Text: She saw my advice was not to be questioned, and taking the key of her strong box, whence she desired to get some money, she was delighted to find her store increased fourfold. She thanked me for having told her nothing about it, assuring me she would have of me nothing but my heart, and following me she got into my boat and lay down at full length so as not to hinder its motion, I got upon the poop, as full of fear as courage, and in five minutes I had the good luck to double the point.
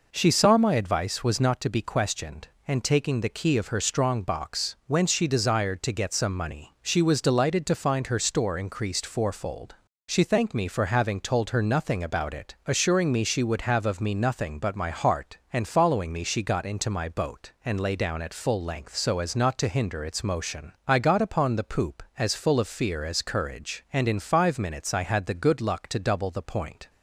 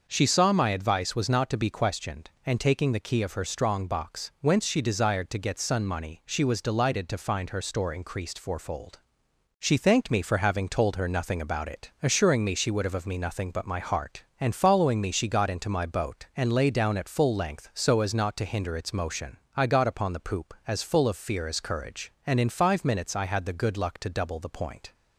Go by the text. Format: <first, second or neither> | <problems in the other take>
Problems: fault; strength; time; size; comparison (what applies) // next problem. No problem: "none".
first | starts louder than the rest; noticeable; until 1.1 s; 6 dB // says "sun" for "some"; at 5.5 s